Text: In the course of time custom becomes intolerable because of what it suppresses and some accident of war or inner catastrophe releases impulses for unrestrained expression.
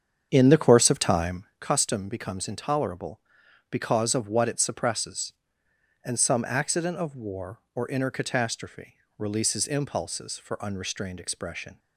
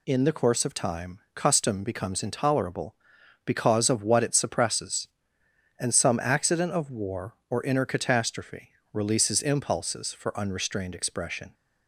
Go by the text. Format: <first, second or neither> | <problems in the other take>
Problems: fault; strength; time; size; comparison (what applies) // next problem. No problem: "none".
second | starts louder than the rest; strong; until 1.6 s; 7.5 dB // pauses between "time" and "custom"; slight; at 1.4 s; 0.16 s long; slight in the second // pauses between "catastrophe" and "releases"; slight; at 8.9 s; 0.20 s long; slight in the second